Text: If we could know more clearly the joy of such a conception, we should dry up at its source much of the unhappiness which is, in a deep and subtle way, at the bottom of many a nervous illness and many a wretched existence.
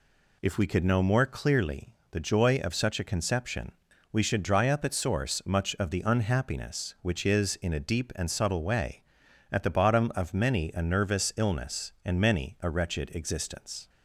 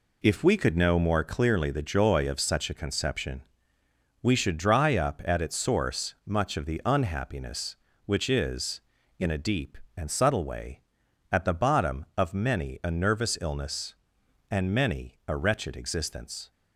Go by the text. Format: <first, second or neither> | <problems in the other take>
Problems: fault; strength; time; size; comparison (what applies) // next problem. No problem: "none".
second | pauses between "clearly" and "the"; slight; at 1.8 s; 0.22 s long // skips "its"; at 4.9 s